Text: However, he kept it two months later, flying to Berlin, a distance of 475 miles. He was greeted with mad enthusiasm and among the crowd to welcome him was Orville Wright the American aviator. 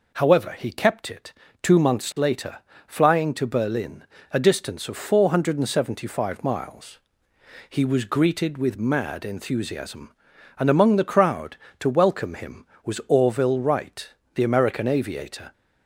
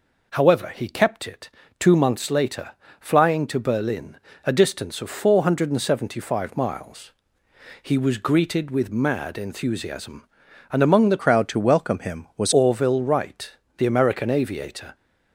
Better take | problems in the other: first | pauses between "it" and "two"; slight; at 1.4 s; 0.30 s long; slight in the first // changes voice from "crowd" to "was"; from 11.2 to 12.5 s; 1.3 s long // pauses between "Wright" and "the"; slight; at 13.5 s; 0.26 s long; slight in the first

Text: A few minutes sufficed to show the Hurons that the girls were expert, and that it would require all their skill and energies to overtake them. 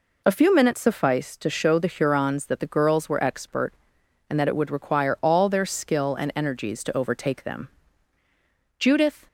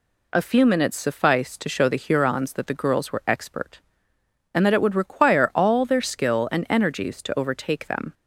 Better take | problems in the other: second | goes on to say "Judith"; slight; from 8.7 s on; 0.48 s long

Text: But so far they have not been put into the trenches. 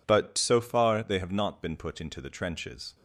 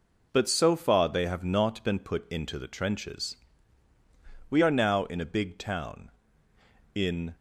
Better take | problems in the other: first | goes on to say "We are now in a big town in"; strong; from 4.4 s on; 2.8 s long

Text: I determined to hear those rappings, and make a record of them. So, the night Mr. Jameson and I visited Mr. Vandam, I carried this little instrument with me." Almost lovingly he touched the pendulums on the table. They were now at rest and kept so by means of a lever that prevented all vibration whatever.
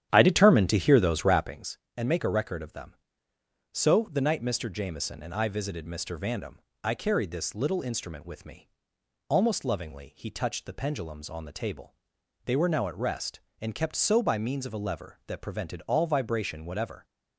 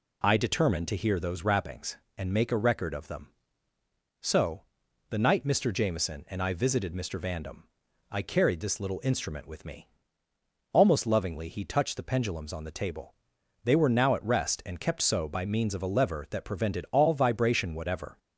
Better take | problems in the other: second | starts louder than the rest; strong; until 1.5 s; 10.5 dB

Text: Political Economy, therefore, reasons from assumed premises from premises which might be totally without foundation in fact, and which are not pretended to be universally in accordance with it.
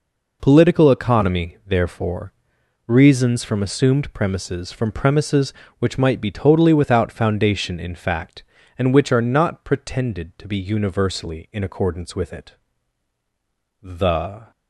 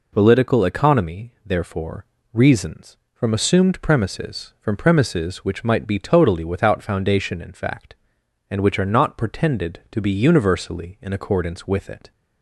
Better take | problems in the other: second | goes on to say "The"; noticeable; from 13.8 s on; 0.68 s long

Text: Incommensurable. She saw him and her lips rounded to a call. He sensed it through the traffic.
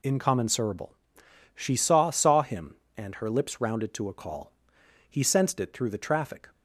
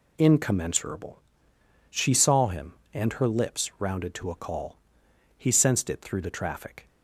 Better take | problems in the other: second | says "saw" twice; at 2.0 s

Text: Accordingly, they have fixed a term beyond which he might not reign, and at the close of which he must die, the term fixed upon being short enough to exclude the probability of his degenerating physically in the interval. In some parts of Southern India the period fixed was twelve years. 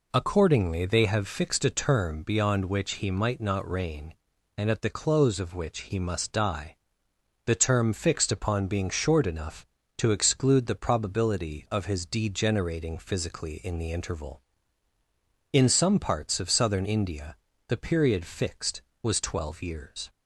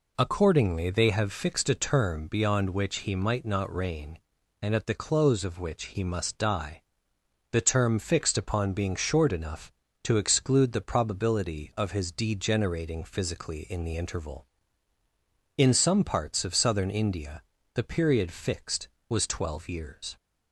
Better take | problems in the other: neither | pauses between "India" and "the"; slight; the same in both

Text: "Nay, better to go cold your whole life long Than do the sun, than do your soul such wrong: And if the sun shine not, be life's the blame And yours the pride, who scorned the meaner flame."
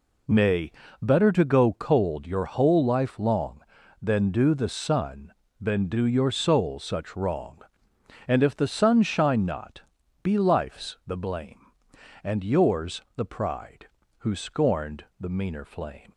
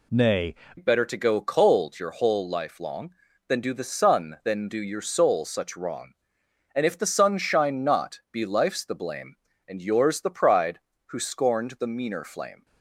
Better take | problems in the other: first | changes voice at "better"; from 0.7 s on; 11.9 s long

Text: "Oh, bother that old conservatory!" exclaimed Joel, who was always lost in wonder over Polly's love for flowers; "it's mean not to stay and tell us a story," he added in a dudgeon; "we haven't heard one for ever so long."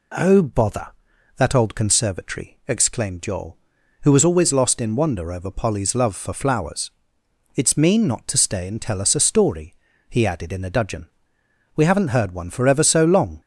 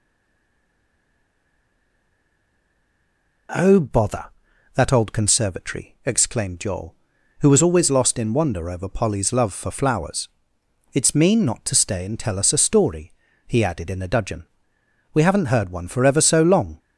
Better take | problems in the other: first | stays silent before the first word; strong; until 3.4 s; 3.4 s long

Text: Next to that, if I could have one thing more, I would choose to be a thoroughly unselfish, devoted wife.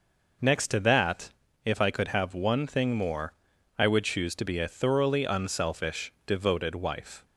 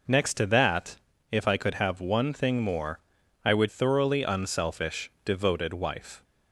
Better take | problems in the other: first | skips "choose to be a"; at 3.6 s

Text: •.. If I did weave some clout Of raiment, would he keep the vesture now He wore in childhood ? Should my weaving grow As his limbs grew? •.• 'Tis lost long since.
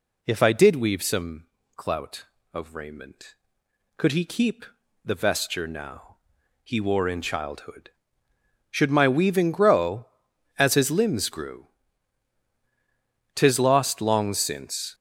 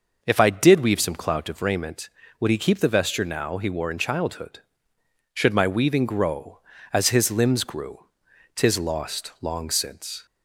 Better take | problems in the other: second | pauses between "some" and "clout"; slight; at 1.4 s; 0.28 s long // says "could" for "would"; at 3.9 s // pauses between "keep" and "the"; slight; at 4.6 s; 0.36 s long // pauses between "now" and "He"; at 6.1 s; 0.44 s long

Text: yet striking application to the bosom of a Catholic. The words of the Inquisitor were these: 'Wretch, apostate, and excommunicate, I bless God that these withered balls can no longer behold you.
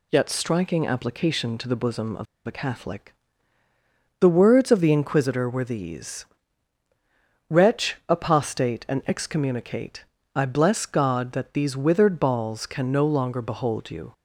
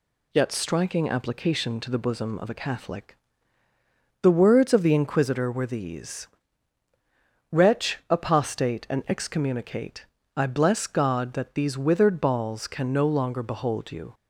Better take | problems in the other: second | pauses between "of" and "a"; slight; at 2.2 s; 0.21 s long

